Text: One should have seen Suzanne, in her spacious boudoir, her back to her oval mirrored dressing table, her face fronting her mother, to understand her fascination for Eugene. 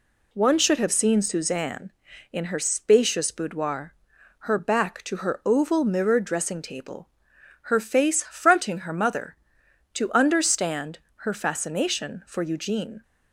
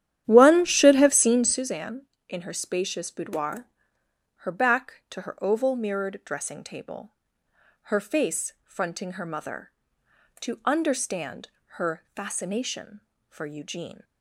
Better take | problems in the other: first | starts louder than the rest; strong; until 1.7 s; 11 dB // pauses between "understand" and "her"; slight; at 11.4 s; 0.28 s long; slight in the first

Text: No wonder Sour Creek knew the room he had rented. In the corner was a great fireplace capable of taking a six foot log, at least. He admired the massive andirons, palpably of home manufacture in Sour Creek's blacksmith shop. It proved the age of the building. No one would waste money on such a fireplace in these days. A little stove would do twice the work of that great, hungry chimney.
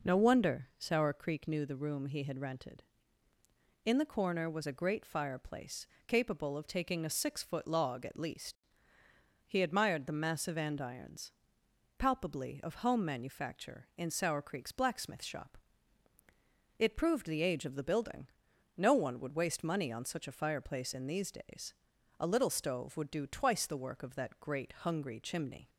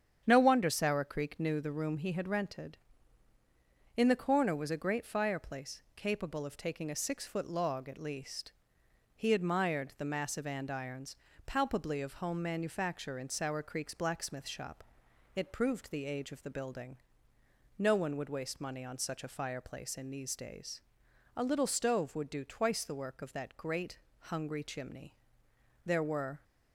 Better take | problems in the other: first | starts louder than the rest; strong; until 1.2 s; 8.5 dB // pauses between "fireplace" and "capable"; slight; at 5.8 s; 0.16 s long; slight in the first // goes on to say "There were"; from 25.8 s on; 0.58 s long

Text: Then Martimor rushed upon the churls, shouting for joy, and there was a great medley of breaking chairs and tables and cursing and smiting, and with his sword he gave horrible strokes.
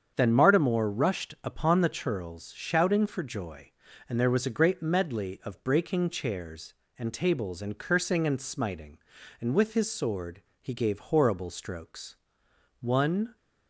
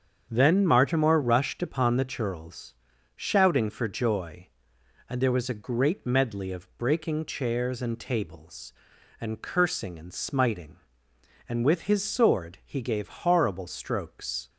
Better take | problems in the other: second | starts louder than the rest; strong; until 1.1 s; 7.5 dB; strong in the second // pauses between "sword" and "he"; slight; at 10.4 s; 0.20 s long // goes on to say "One"; from 12.8 s on; 0.54 s long

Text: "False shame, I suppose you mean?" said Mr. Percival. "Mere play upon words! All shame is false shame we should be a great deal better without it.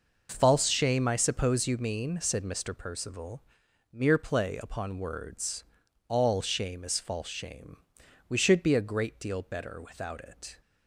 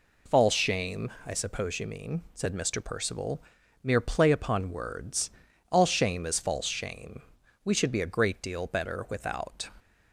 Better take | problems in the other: first | pauses between "shame" and "we"; at 7.2 s; 0.40 s long; noticeable in the first // stops before "it"; at 9.7 s

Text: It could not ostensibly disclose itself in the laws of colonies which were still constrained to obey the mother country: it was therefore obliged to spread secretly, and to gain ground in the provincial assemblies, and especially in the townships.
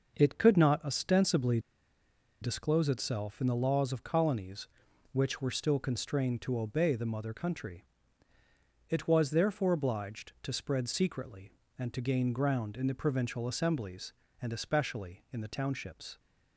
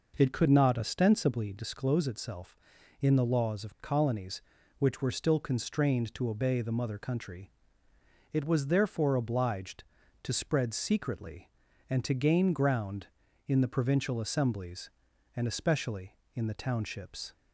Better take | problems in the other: second | pauses between "ostensibly" and "disclose"; noticeable; at 1.5 s; 0.82 s long

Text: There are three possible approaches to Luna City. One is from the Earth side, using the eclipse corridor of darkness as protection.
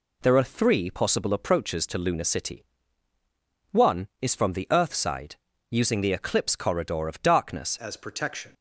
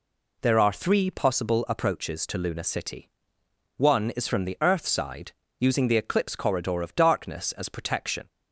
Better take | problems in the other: second | changes voice at "as"; from 7.7 s on; 0.8 s long

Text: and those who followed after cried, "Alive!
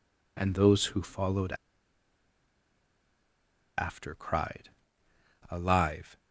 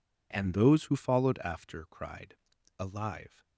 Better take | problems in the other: second | pauses between "followed" and "after"; strong; at 1.5 s; 2.2 s long

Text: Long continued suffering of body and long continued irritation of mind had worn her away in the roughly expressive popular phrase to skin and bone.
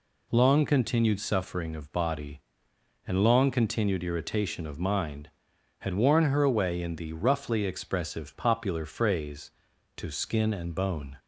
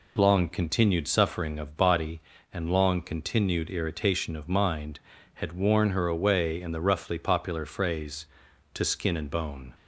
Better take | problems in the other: first | skips "expressive"; at 7.1 s

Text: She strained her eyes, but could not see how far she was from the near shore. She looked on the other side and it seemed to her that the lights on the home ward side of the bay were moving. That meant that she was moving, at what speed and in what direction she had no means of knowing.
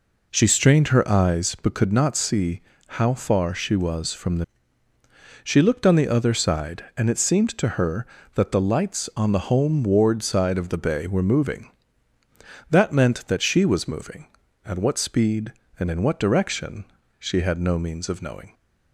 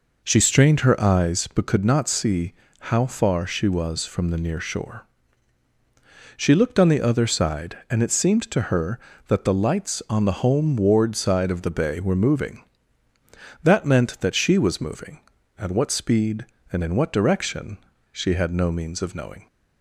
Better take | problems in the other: second | pauses between "see" and "how"; slight; at 2.6 s; 0.26 s long; slight in the second // skips "near shore"; at 4.9 s // pauses between "direction" and "she"; slight; at 16.8 s; 0.34 s long; slight in the second

